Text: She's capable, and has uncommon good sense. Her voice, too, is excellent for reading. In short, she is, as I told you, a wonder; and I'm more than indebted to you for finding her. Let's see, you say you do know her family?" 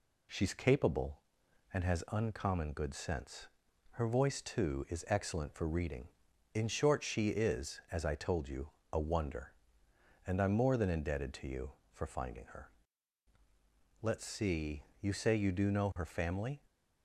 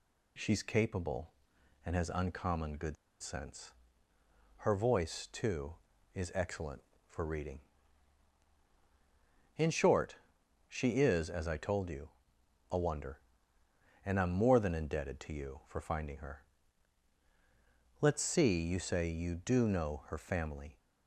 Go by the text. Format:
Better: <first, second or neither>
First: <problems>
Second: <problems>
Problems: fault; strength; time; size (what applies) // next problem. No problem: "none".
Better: first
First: none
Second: pauses between "good" and "sense"; slight; at 2.9 s; 0.25 s long